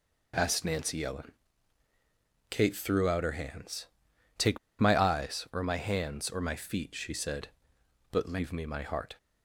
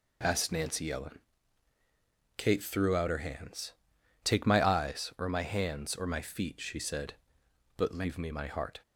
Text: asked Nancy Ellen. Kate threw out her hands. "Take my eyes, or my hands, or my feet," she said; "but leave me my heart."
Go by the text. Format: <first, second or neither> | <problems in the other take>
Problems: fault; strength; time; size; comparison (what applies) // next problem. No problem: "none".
second | pauses between "Take" and "my"; slight; at 4.5 s; 0.20 s long